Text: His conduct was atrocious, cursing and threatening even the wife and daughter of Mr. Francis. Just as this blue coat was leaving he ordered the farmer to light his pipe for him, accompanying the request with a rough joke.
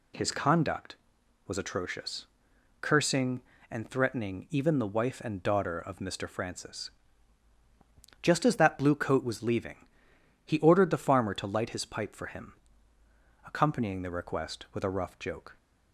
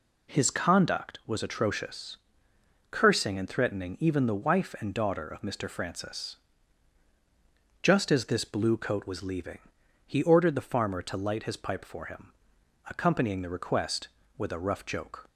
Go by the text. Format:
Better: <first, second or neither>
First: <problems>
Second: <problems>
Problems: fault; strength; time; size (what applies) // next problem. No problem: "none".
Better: second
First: says "that" for "this"; at 8.5 s // pauses between "leaving" and "he"; noticeable; at 9.8 s; 0.58 s long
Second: pauses between "leaving" and "he"; noticeable; at 9.5 s; 0.48 s long